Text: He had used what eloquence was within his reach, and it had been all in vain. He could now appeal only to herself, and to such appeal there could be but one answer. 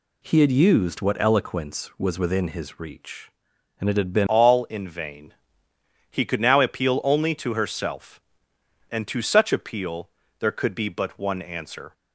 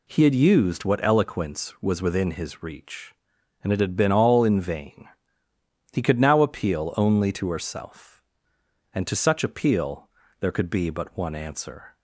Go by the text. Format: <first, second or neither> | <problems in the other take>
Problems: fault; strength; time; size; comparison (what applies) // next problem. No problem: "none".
second | changes voice at "all"; from 4.2 s on; 7.7 s long // pauses between "appeal" and "there"; slight; at 10.0 s; 0.30 s long; slight in the second